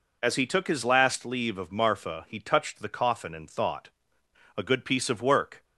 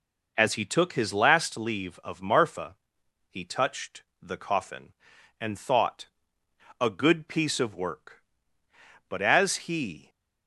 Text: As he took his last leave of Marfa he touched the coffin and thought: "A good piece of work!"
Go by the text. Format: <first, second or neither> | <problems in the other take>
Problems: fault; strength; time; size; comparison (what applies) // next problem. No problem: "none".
first | pauses between "Marfa" and "he"; noticeable; at 2.7 s; 0.54 s long // pauses between "touched" and "the"; slight; at 4.0 s; 0.16 s long // goes on to say "But as he"; noticeable; from 9.0 s on; 1.0 s long